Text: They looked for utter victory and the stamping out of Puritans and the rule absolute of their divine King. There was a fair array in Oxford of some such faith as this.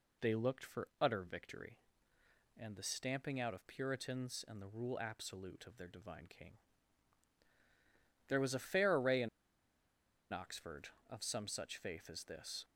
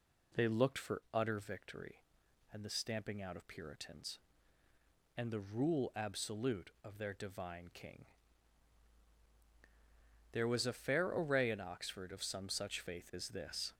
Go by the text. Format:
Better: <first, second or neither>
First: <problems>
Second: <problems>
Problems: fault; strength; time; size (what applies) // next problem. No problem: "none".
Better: second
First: pauses between "in" and "Oxford"; at 9.2 s; 1.0 s long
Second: none